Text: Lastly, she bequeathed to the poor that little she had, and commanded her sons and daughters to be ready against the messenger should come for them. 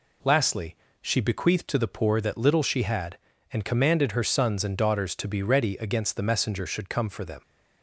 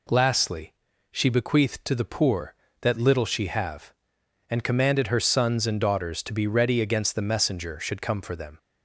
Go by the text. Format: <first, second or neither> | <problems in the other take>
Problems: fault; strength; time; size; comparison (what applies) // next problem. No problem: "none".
first | says "have" for "had"; at 3.4 s